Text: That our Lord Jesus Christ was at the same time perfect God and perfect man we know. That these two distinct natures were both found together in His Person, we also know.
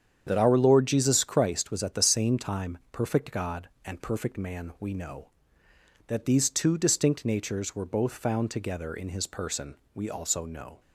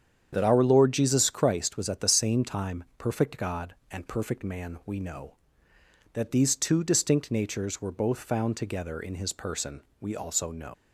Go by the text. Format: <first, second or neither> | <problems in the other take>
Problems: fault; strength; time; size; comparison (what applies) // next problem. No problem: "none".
first | starts louder than the rest; strong; until 1.3 s; 8 dB; strong in the first // leaves "know" unfinished; at 10.7 s; 115 ms